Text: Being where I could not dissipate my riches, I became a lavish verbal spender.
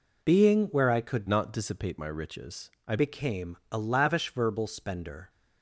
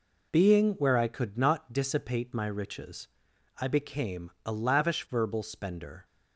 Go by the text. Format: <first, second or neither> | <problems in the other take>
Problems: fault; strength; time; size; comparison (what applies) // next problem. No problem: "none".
second | changes voice from "not" to "I"; from 1.2 to 2.9 s; 1.7 s long